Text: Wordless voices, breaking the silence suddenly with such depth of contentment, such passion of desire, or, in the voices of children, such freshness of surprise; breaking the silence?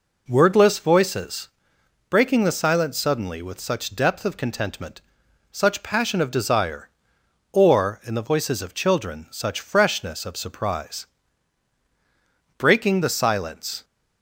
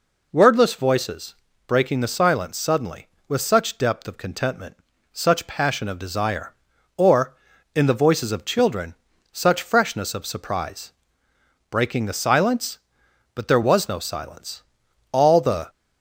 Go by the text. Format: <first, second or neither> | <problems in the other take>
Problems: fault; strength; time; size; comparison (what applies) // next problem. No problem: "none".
first | goes on to say "But there was no silence all the"; strong; from 13.3 s on; 2.3 s long